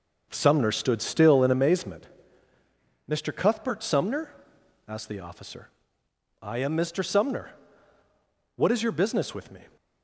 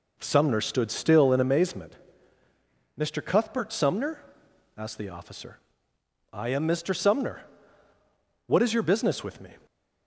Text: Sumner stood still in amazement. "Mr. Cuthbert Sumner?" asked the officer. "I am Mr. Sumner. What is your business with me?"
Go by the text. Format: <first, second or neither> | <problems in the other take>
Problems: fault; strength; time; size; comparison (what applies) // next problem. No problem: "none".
second | gets quieter; throughout; 7 dB